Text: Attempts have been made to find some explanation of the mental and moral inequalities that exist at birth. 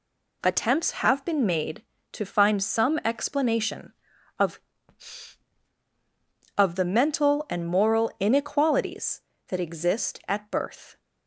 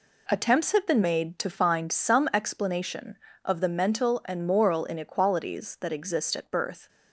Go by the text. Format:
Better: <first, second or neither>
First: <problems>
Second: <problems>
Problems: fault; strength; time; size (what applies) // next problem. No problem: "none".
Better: second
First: says "of" twice; at 6.5 s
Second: none